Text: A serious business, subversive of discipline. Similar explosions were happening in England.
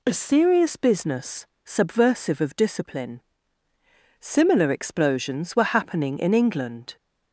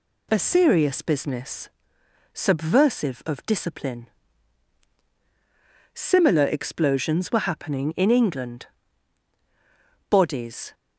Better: first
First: none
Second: goes on to say "Bodies"; noticeable; from 10.1 s on; 0.62 s long

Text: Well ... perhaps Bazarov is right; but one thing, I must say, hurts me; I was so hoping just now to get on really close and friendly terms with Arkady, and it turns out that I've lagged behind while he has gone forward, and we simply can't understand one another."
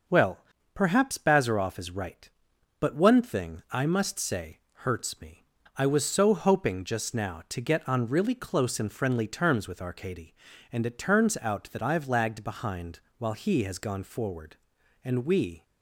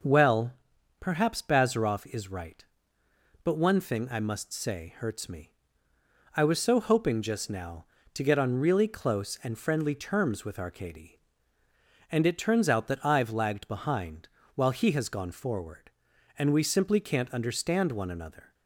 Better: second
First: pauses between "behind" and "while"; slight; at 12.9 s; 0.18 s long // stops before "simply can't understand one another"; at 15.6 s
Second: pauses between "behind" and "while"; slight; at 14.2 s; 0.28 s long

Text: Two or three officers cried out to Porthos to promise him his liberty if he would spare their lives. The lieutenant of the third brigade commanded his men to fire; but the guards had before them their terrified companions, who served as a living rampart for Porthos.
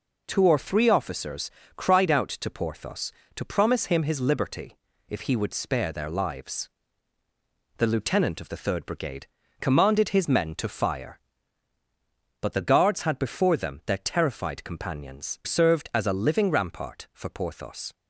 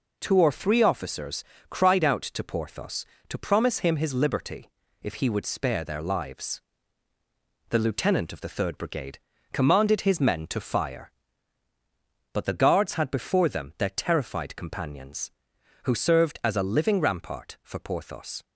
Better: second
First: pauses between "officers" and "cried"; slight; at 1.5 s; 0.26 s long // pauses between "liberty" and "if"; slight; at 4.7 s; 0.32 s long // pauses between "brigade" and "commanded"; slight; at 9.2 s; 0.34 s long // skips "who"; at 15.4 s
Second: pauses between "officers" and "cried"; slight; at 1.4 s; 0.26 s long // pauses between "liberty" and "if"; slight; at 4.6 s; 0.32 s long // pauses between "brigade" and "commanded"; slight; at 9.1 s; 0.34 s long

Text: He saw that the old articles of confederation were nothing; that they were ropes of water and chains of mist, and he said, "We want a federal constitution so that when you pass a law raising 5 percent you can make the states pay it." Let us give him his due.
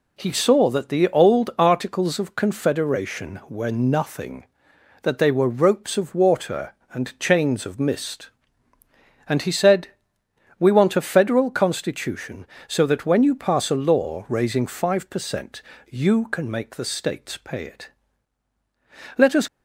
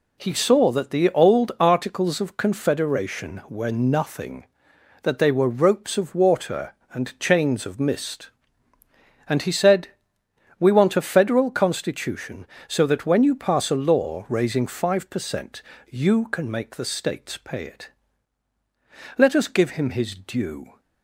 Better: second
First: pauses between "percent" and "you"; slight; at 15.6 s; 0.26 s long // stops before "give him his due"; at 19.4 s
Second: pauses between "percent" and "you"; slight; at 15.6 s; 0.26 s long

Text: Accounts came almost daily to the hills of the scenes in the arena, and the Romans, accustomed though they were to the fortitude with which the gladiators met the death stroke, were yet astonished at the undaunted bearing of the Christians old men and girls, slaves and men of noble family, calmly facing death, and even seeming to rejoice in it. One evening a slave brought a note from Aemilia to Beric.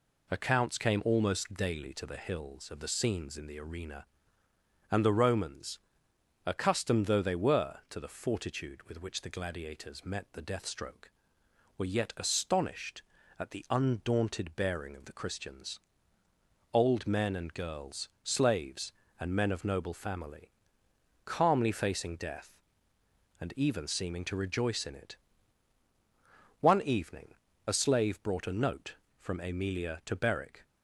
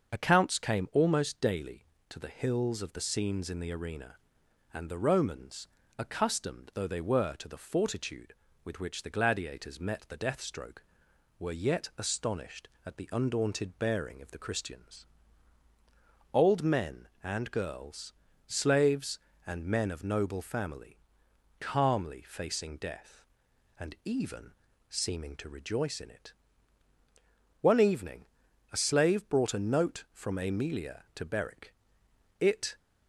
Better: first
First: pauses between "Christians" and "old"; noticeable; at 15.7 s; 0.92 s long // pauses between "evening" and "a"; slight; at 27.3 s; 0.32 s long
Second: starts louder than the rest; until 1.1 s; 6.5 dB // pauses between "Christians" and "old"; strong; at 15.0 s; 1.2 s long // pauses between "even" and "seeming"; at 24.5 s; 0.38 s long // pauses between "evening" and "a"; noticeable; at 28.2 s; 0.46 s long // goes on to say "It"; slight; from 32.3 s on; 0.38 s long

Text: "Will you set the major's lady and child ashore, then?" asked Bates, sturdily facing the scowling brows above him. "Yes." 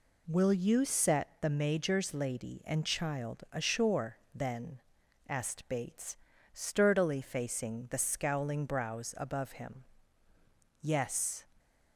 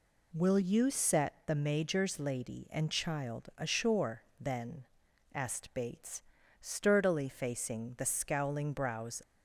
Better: first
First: none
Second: stops before "above him Yes"; at 9.2 s

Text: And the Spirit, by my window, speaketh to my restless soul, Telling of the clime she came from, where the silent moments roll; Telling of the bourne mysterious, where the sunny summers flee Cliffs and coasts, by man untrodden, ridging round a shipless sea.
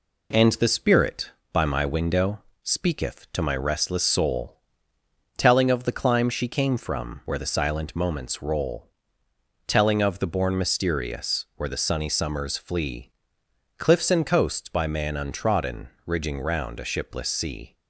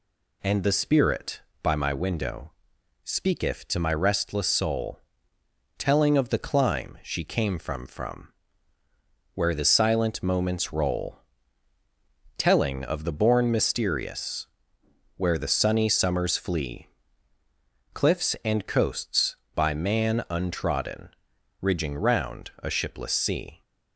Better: first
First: pauses between "flee" and "Cliffs"; noticeable; at 13.0 s; 0.70 s long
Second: says "from" twice; at 7.8 s // pauses between "flee" and "Cliffs"; at 16.8 s; 1.0 s long

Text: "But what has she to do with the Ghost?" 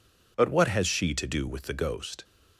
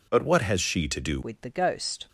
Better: first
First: none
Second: changes voice at "with"; from 1.2 s on; 0.8 s long

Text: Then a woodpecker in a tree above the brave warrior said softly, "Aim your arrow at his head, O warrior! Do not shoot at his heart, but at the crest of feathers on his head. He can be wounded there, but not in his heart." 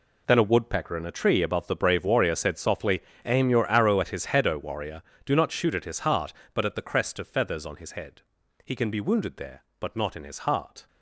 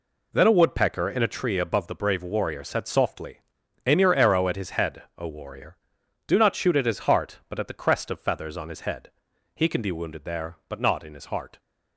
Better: second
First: gets quieter; strong; throughout; 13 dB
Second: none

